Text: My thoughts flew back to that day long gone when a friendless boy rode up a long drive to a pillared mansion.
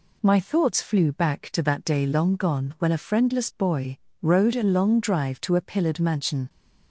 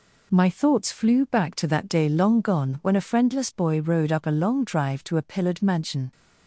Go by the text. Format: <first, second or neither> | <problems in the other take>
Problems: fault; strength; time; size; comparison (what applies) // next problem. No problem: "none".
second | pauses between "boy" and "rode"; slight; at 3.9 s; 0.22 s long // skips "up"; at 4.5 s